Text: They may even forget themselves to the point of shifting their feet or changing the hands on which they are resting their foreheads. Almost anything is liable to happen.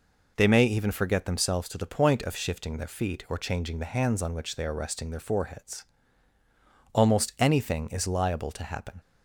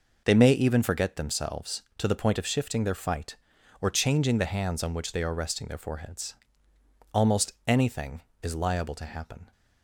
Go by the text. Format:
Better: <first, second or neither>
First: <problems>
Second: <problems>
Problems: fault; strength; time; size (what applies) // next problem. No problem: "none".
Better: first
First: none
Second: says "fight" for "feet"; at 2.9 s